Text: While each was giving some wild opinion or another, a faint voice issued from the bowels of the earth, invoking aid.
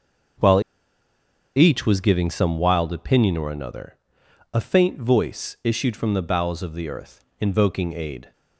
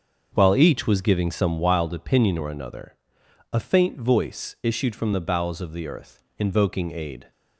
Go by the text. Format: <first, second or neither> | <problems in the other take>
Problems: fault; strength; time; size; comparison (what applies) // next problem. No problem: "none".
second | starts louder than the rest; until 2.3 s; 6.5 dB; also in the second // pauses between "While" and "each"; noticeable; at 0.6 s; 0.93 s long